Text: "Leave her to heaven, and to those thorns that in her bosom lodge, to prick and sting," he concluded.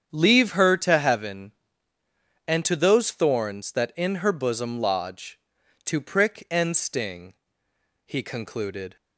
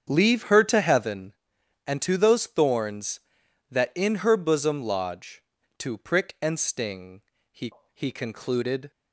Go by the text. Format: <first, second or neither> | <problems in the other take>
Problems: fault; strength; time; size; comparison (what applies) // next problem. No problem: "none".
first | starts louder than the rest; strong; until 1.1 s; 7.5 dB; strong in the first // says "he" twice; at 7.9 s